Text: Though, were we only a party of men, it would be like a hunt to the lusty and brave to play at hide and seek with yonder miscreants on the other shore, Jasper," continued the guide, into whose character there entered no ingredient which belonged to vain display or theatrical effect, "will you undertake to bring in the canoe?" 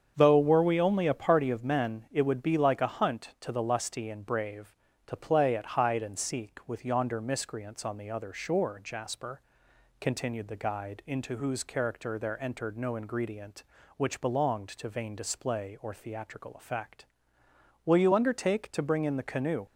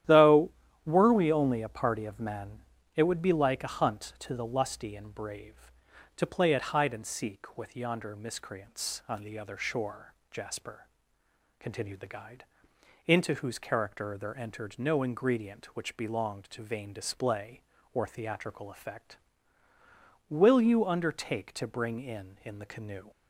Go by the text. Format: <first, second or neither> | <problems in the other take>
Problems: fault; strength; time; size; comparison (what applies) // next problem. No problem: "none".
first | starts louder than the rest; strong; until 1.3 s; 11.5 dB; strong in the first // says "in" twice; at 22.4 s